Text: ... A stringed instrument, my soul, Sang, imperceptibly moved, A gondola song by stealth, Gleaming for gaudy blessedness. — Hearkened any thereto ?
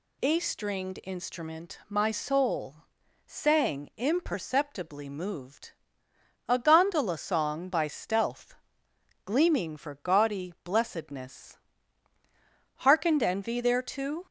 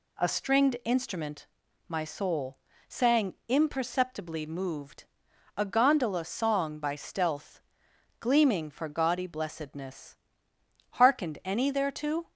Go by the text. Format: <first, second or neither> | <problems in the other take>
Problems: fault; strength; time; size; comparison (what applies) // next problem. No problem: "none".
second | says "envy" for "any"; at 13.2 s